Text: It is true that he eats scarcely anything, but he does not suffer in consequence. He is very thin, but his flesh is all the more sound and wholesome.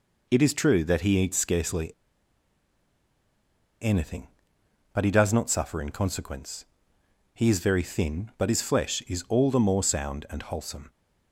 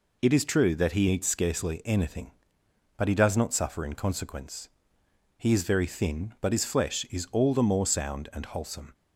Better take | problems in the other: second | pauses between "scarcely" and "anything"; strong; at 1.8 s; 1.9 s long

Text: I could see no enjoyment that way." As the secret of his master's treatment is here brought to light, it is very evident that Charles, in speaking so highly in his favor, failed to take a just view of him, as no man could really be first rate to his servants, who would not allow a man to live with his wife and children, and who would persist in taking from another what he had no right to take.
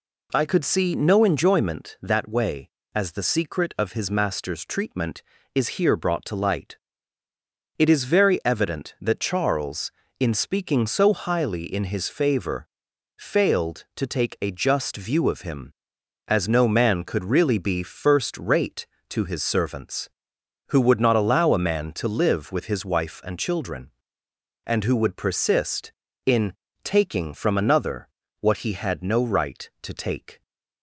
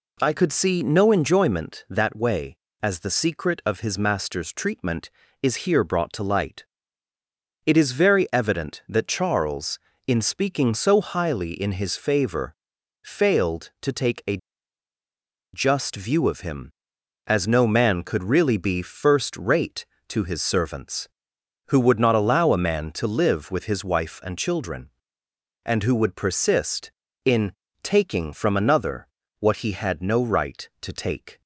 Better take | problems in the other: first | pauses between "a" and "just"; at 14.3 s; 1.1 s long // pauses between "in" and "taking"; slight; at 27.5 s; 0.32 s long; slight in the first // pauses between "another" and "what"; slight; at 29.0 s; 0.32 s long; slight in the first

